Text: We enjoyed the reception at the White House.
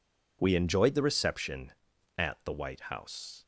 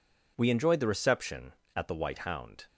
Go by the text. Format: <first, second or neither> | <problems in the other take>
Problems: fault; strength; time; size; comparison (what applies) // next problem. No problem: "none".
first | says "Hound" for "House"; at 2.1 s